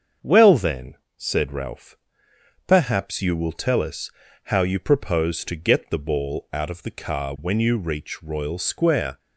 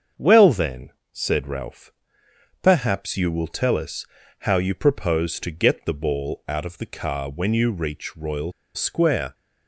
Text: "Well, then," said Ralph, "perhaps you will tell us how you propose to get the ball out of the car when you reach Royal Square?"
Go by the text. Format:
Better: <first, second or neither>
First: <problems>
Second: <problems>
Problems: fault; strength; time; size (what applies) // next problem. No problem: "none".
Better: first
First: starts louder than the rest; until 1.4 s; 7 dB // pauses between "us" and "how"; slight; at 4.0 s; 0.34 s long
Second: starts louder than the rest; until 1.3 s; 7 dB // pauses between "us" and "how"; slight; at 4.0 s; 0.34 s long // pauses between "Royal" and "Square"; slight; at 8.5 s; 0.24 s long